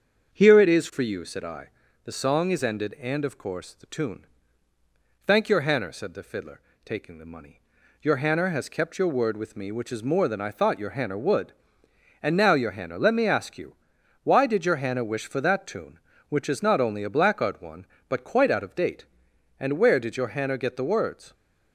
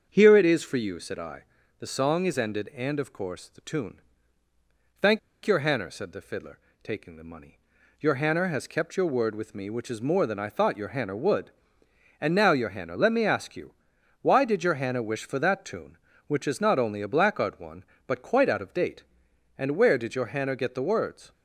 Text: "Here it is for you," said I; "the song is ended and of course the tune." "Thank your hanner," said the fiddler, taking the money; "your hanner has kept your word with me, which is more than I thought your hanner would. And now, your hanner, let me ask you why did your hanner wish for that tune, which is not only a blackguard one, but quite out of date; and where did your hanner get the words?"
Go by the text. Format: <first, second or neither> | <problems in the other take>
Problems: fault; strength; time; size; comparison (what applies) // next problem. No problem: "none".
first | starts louder than the rest; until 1.1 s; 7 dB; also in the first // pauses between "Thank" and "your"; slight; at 5.1 s; 0.26 s long // pauses between "you" and "why"; noticeable; at 13.7 s; 0.48 s long; noticeable in the first